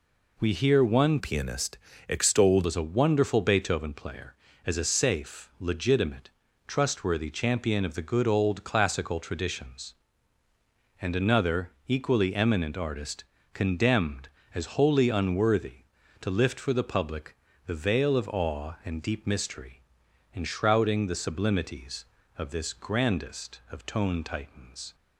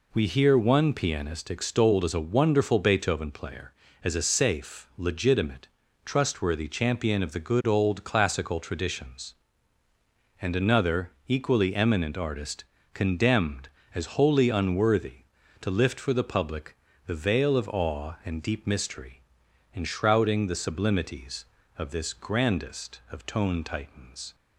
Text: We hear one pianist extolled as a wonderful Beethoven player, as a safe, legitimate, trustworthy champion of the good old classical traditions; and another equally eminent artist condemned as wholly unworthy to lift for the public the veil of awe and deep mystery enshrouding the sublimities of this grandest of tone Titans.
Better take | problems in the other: second | changes voice from "pianist" to "extolled"; from 1.1 to 2.6 s; 1.5 s long // pauses between "pianist" and "extolled"; slight; at 1.7 s; 0.32 s long // pauses between "artist" and "condemned"; slight; at 13.2 s; 0.28 s long; slight in the second // pauses between "public" and "the"; slight; at 17.3 s; 0.30 s long; slight in the second // pauses between "mystery" and "enshrouding"; noticeable; at 19.8 s; 0.52 s long; noticeable in the second

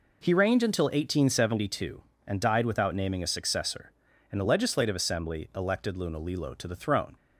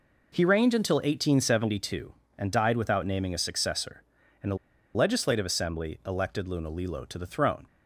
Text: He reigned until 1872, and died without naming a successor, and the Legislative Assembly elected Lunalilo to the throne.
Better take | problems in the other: first | pauses between "the" and "Legislative"; at 4.5 s; 0.39 s long

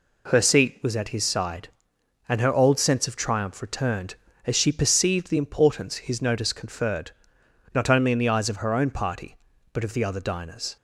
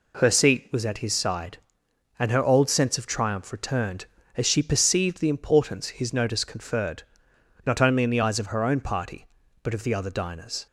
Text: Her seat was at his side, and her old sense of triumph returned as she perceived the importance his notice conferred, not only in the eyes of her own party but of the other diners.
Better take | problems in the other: neither | none

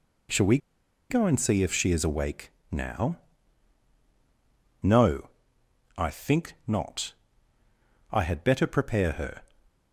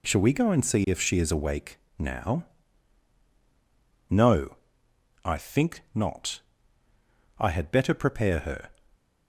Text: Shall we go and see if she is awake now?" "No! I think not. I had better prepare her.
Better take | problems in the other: second | pauses between "we" and "go"; noticeable; at 0.5 s; 0.52 s long // pauses between "awake" and "now"; slight; at 2.5 s; 0.20 s long; slight in the second

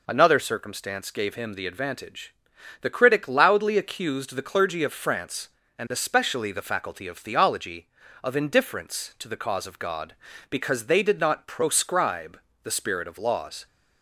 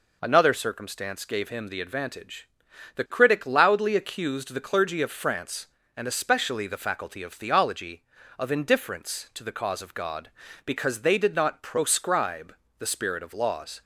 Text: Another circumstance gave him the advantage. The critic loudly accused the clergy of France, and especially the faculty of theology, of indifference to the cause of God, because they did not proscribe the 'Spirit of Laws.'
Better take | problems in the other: neither | pauses between "proscribe" and "the"; slight; the same in both

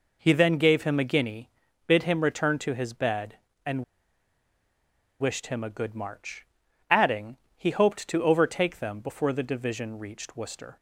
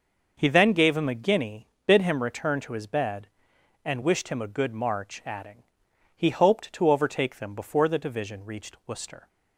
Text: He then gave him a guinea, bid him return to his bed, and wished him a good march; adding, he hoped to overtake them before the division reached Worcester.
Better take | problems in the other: second | pauses between "and" and "wished"; strong; at 3.8 s; 1.3 s long

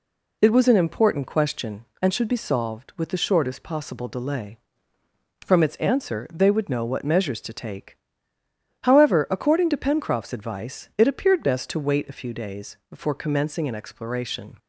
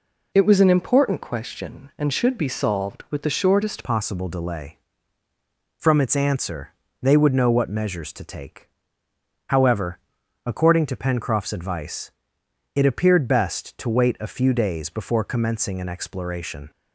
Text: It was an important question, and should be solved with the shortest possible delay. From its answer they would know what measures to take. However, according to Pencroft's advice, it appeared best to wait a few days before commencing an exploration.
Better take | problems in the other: first | changes voice at "possible"; from 3.8 s on; 12.9 s long // pauses between "answer" and "they"; slight; at 6.7 s; 0.28 s long

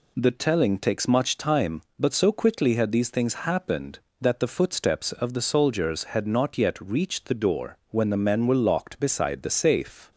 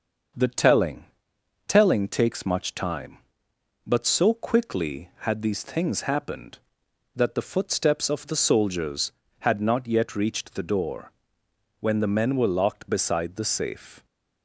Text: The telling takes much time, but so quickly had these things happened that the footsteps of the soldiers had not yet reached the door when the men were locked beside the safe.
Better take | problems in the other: first | starts louder than the rest; until 1.9 s; 6.5 dB // says "telling" twice; at 1.6 s // pauses between "door" and "when"; noticeable; at 11.1 s; 0.70 s long

